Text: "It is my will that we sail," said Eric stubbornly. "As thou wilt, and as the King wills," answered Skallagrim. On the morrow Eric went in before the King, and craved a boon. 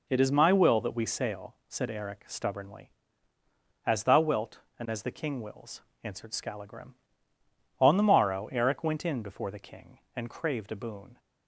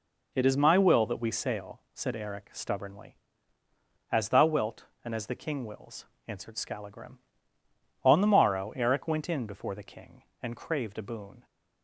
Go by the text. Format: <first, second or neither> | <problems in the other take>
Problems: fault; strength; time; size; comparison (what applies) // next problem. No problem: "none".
neither | none